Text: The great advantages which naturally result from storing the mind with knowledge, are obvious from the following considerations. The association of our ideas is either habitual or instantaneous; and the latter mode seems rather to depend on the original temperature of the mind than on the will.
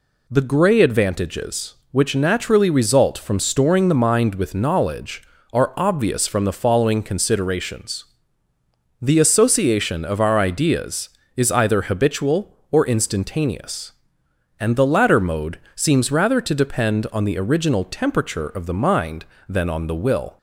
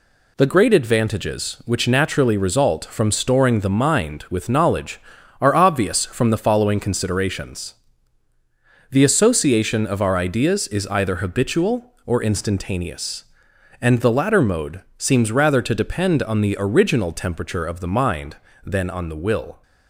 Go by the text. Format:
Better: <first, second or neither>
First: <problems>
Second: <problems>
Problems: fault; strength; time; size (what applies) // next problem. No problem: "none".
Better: second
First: says "grey" for "great"; at 0.4 s // pauses between "mode" and "seems"; slight; at 15.5 s; 0.18 s long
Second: pauses between "mode" and "seems"; slight; at 14.8 s; 0.16 s long